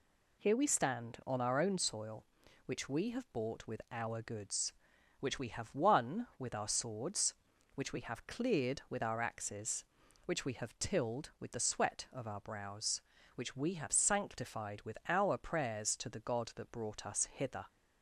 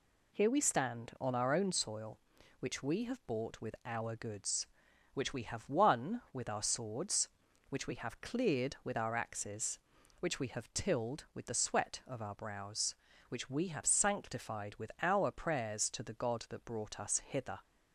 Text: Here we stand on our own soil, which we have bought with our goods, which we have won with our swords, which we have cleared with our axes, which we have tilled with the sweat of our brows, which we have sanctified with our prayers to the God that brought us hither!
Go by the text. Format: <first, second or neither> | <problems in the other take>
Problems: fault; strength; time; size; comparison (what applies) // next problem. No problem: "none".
neither | none